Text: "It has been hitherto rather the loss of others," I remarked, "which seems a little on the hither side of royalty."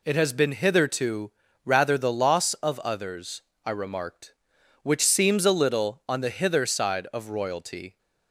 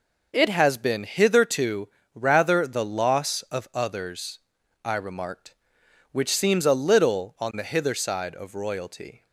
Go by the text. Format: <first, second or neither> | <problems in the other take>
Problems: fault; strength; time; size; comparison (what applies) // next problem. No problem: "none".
neither | pauses between "hitherto" and "rather"; slight; the same in both